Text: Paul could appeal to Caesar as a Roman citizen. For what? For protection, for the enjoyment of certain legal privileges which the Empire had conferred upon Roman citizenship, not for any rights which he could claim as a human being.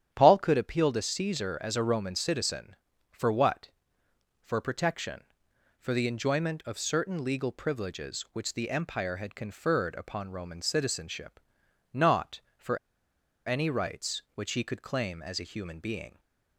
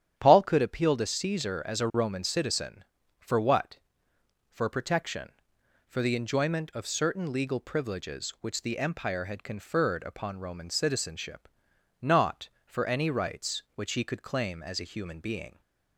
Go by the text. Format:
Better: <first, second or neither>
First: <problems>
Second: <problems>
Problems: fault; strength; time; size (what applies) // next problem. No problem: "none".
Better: second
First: starts louder than the rest; strong; until 1.1 s; 9.5 dB // pauses between "for" and "any"; noticeable; at 12.7 s; 0.68 s long // stays silent after the last word; slight; from 16.0 s on; 0.5 s long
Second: starts louder than the rest; strong; until 1.1 s; 9.5 dB